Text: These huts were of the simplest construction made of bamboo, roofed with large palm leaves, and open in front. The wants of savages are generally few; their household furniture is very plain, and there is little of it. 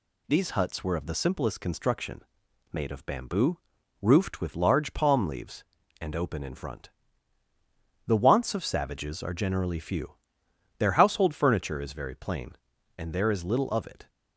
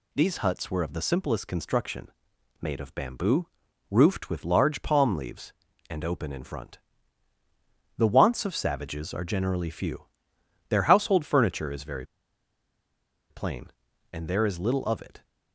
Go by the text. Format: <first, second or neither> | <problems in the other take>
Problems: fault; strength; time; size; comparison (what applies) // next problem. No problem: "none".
first | pauses between "construction" and "made"; noticeable; at 2.0 s; 0.50 s long; noticeable in the first // pauses between "very" and "plain"; strong; at 12.0 s; 1.2 s long